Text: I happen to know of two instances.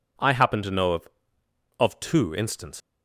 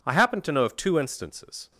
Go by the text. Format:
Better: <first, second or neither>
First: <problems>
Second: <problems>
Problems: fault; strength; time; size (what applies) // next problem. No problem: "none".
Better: second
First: says "of" twice; at 1.7 s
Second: none